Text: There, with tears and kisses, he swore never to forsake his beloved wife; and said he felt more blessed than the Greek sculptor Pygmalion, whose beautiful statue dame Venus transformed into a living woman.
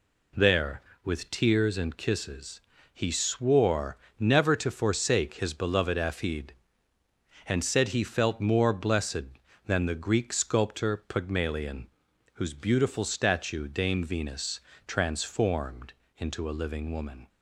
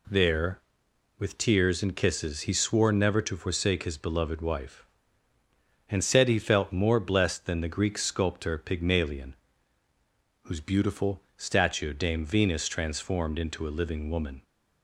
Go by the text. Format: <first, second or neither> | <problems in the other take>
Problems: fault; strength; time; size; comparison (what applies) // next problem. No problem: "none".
second | pauses between "swore" and "never"; slight; at 3.9 s; 0.22 s long // says "afid" for "wife"; at 5.9 s // pauses between "Venus" and "transformed"; slight; at 14.5 s; 0.30 s long // pauses between "transformed" and "into"; slight; at 15.9 s; 0.26 s long